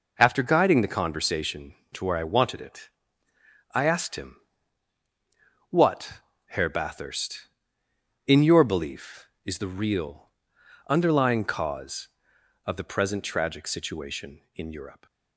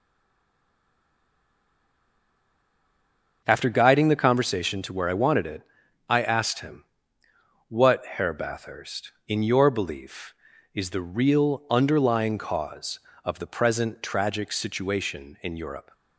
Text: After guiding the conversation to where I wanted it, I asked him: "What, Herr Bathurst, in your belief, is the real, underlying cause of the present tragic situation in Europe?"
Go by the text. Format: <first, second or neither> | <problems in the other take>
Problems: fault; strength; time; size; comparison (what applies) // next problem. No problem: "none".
first | stays silent before the first word; strong; until 3.4 s; 3.4 s long